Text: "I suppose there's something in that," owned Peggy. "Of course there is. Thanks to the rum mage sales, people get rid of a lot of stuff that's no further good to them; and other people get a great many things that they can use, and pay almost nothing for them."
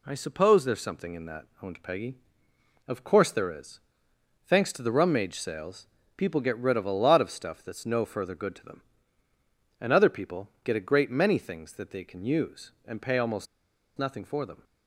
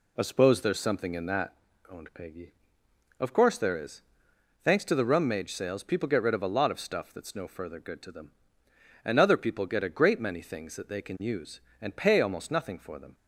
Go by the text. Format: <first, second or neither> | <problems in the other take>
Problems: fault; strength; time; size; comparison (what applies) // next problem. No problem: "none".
second | pauses between "people" and "get"; slight; at 10.4 s; 0.16 s long // pauses between "almost" and "nothing"; noticeable; at 13.4 s; 0.51 s long